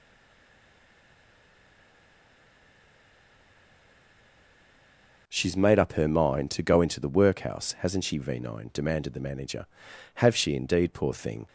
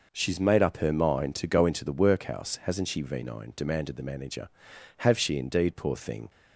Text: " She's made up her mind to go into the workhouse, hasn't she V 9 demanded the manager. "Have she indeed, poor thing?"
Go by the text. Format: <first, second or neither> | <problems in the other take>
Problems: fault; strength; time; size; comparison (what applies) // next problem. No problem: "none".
second | stays silent before the first word; strong; until 5.2 s; 5.2 s long